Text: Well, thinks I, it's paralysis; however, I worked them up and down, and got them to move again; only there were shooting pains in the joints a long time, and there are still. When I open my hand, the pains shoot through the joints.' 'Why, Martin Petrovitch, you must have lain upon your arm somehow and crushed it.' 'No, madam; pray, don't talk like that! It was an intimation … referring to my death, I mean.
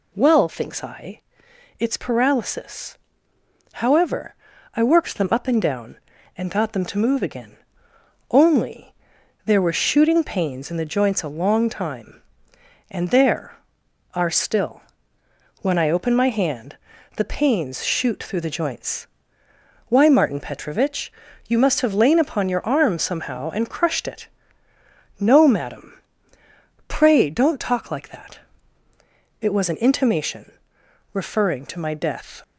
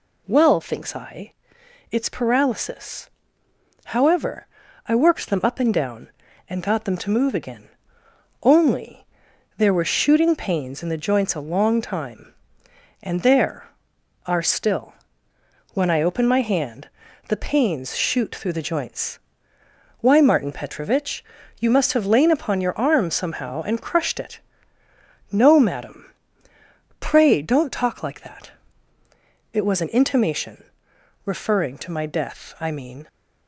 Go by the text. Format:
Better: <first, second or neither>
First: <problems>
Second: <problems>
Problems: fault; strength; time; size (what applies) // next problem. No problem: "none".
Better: second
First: pauses between "only" and "there"; noticeable; at 8.9 s; 0.54 s long // stops before "I mean"; at 32.4 s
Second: pauses between "only" and "there"; noticeable; at 9.0 s; 0.54 s long